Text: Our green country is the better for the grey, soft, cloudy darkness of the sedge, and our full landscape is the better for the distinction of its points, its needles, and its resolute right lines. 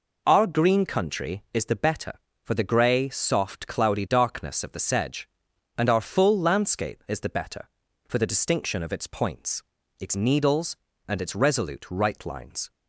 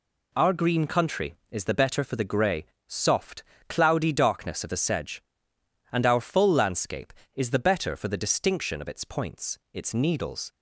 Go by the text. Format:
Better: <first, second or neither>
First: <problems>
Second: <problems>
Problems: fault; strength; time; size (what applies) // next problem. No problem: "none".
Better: first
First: none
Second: stops before "and its resolute right lines"; at 10.5 s